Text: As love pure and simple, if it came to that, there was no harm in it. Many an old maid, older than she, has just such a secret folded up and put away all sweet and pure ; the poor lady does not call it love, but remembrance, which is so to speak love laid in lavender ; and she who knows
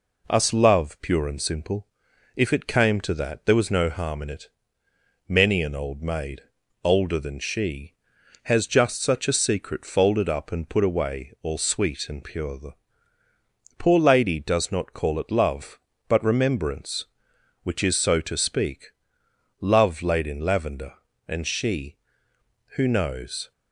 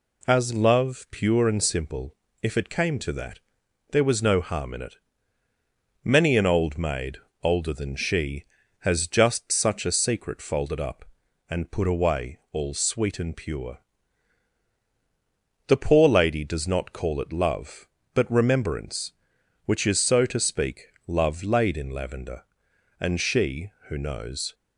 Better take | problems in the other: second | says "Us" for "As"; at 0.2 s // pauses between "the" and "poor"; at 12.7 s; 1.0 s long // pauses between "speak" and "love"; noticeable; at 18.8 s; 0.74 s long; slight in the second

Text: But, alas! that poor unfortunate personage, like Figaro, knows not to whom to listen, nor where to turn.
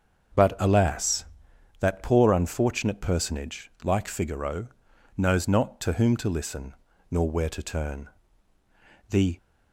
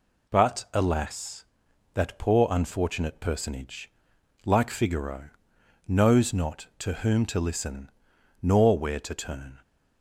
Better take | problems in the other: second | starts louder than the rest; until 1.9 s; 7 dB // goes on to say "The"; slight; from 9.1 s on; 0.26 s long

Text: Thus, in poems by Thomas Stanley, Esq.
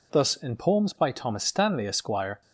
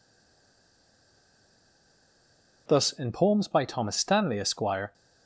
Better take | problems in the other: first | stays silent before the first word; strong; until 2.6 s; 2.6 s long

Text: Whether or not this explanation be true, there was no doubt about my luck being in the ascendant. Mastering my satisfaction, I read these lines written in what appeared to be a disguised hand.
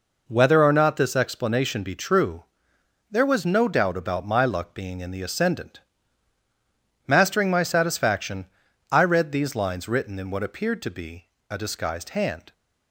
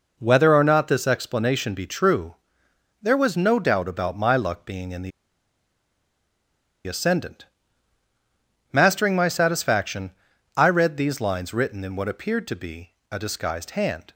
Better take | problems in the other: first | pauses between "the" and "ascendant"; strong; at 5.1 s; 1.7 s long // pauses between "be" and "a"; slight; at 12.9 s; 0.18 s long; slight in the first

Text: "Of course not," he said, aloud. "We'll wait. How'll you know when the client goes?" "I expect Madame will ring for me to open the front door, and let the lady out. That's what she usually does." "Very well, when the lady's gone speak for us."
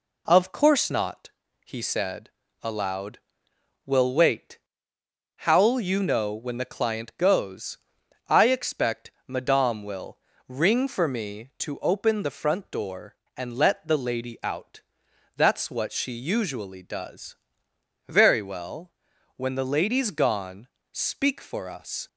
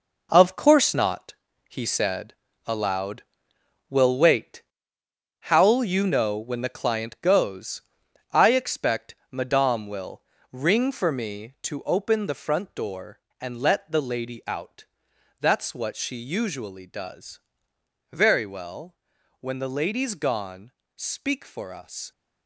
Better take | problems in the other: first | gets quieter; strong; throughout; 8.5 dB // pauses between "expect" and "Madame"; slight; at 9.1 s; 0.16 s long; slight in the first // pauses between "will" and "ring"; slight; at 10.2 s; 0.30 s long; slight in the first // pauses between "gone" and "speak"; slight; at 20.7 s; 0.24 s long; slight in the first

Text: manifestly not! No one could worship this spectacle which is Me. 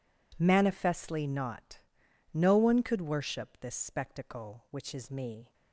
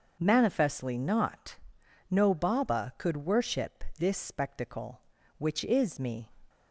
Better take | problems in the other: first | starts louder than the rest; noticeable; until 1.1 s; 6 dB // says "baba" for "one"; at 2.3 s

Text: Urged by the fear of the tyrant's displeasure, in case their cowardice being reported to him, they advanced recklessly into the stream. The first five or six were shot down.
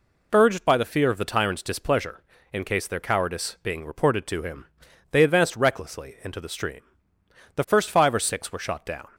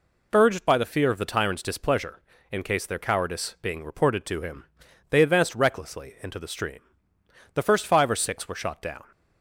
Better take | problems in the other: neither | none

